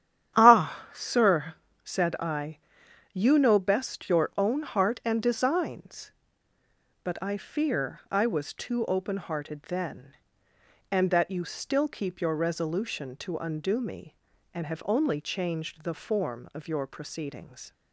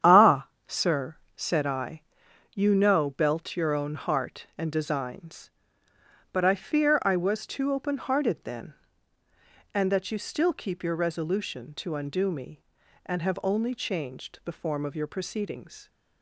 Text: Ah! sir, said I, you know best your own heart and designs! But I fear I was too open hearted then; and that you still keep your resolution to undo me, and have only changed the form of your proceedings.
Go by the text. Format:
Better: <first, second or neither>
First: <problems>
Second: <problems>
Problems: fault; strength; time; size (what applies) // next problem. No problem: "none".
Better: first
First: starts louder than the rest; strong; until 1.4 s; 10 dB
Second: starts louder than the rest; strong; until 1.4 s; 9 dB // says "belt" for "best"; at 3.1 s